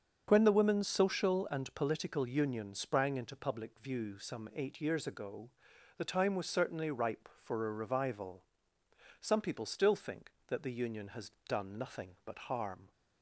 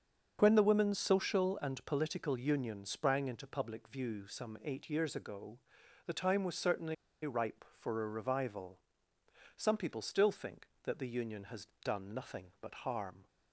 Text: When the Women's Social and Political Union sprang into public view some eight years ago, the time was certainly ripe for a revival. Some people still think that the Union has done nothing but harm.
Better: first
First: starts louder than the rest; until 1.2 s; 7 dB // pauses between "has" and "done"; slight; at 11.3 s; 0.18 s long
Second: starts louder than the rest; until 1.4 s; 6.5 dB // pauses between "certainly" and "ripe"; slight; at 6.9 s; 0.30 s long // pauses between "has" and "done"; slight; at 11.6 s; 0.18 s long

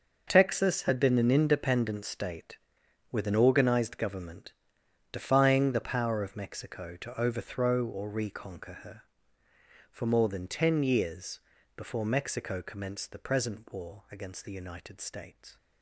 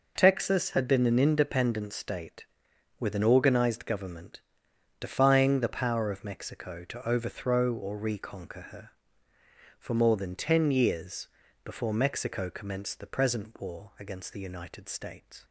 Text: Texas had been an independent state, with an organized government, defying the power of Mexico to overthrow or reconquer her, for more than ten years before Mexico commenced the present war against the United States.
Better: second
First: gets quieter; strong; throughout; 12.5 dB // pauses between "years" and "before"; slight; at 11.4 s; 0.36 s long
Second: pauses between "years" and "before"; slight; at 11.2 s; 0.36 s long

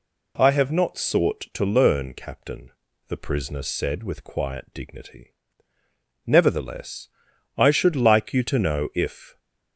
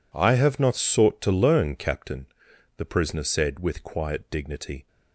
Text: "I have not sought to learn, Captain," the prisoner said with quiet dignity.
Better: second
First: goes on to say "Nevertheless I should like you to know if"; strong; from 6.2 s on; 3.1 s long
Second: none

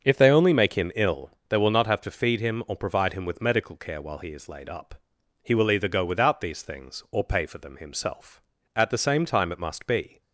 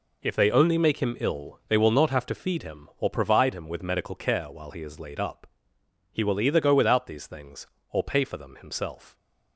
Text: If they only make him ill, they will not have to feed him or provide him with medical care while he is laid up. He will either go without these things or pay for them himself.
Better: second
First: starts louder than the rest; until 1.0 s; 6.5 dB // goes on to say "At the same time it must be"; from 8.7 s on; 1.4 s long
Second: none

